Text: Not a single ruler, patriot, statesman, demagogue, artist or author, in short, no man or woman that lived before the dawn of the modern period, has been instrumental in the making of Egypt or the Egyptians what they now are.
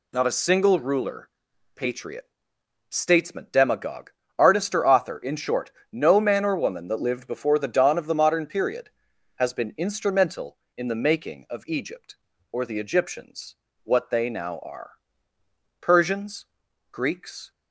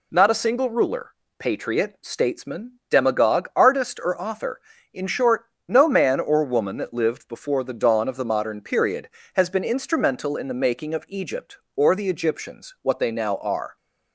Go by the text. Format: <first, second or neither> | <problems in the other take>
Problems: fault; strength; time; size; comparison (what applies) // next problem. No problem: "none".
second | pauses between "Egyptians" and "what"; slight; at 13.5 s; 0.26 s long // goes on to say "Persians Greeks"; strong; from 15.8 s on; 1.7 s long